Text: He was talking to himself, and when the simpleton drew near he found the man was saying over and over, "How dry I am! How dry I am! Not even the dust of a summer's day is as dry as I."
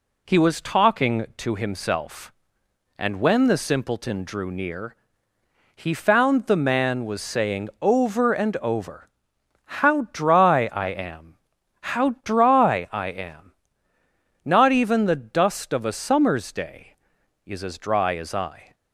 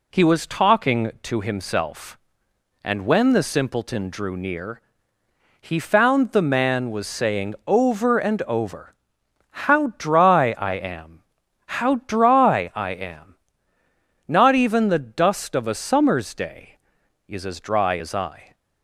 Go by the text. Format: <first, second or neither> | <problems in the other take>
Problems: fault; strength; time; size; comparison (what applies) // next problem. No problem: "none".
neither | pauses between "near" and "he"; noticeable; the same in both